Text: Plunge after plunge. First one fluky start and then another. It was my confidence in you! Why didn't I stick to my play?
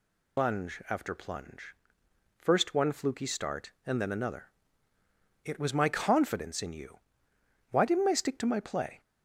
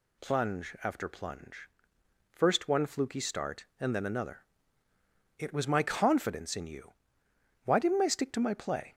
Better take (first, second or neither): second